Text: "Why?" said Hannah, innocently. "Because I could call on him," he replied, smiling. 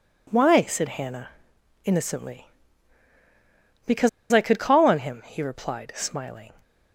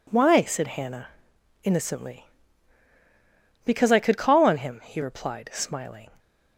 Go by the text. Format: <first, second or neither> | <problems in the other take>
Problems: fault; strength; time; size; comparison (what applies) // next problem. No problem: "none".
second | pauses between "Because" and "I"; slight; at 4.0 s; 0.23 s long